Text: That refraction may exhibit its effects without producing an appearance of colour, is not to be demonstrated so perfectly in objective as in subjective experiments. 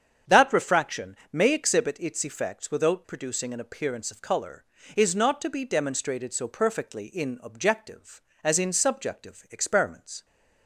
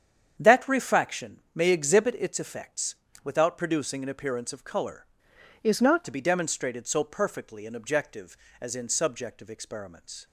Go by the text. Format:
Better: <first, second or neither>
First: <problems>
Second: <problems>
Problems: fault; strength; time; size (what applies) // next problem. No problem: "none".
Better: first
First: starts louder than the rest; strong; until 1.4 s; 7.5 dB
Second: starts louder than the rest; strong; until 1.4 s; 8 dB // pauses between "effects" and "without"; slight; at 2.9 s; 0.30 s long // changes voice from "is" to "not"; from 5.6 to 6.0 s; 0.4 s long